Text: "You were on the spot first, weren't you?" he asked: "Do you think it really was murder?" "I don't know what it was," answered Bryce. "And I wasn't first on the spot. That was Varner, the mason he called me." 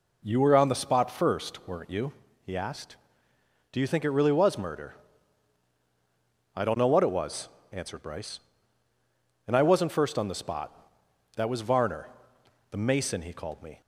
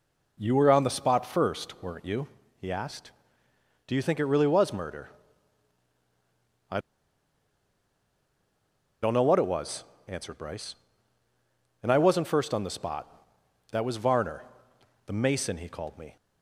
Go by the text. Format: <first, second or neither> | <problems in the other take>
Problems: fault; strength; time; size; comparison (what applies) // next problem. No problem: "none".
first | pauses between "I" and "don't"; strong; at 6.7 s; 2.2 s long